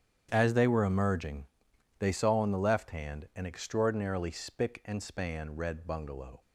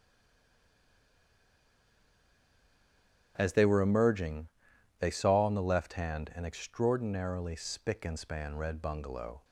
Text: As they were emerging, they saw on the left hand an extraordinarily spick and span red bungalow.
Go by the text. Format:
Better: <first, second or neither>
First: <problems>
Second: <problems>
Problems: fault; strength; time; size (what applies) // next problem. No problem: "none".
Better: first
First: starts louder than the rest; strong; until 1.3 s; 9 dB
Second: stays silent before the first word; strong; until 3.3 s; 3.3 s long // starts louder than the rest; strong; until 4.3 s; 10 dB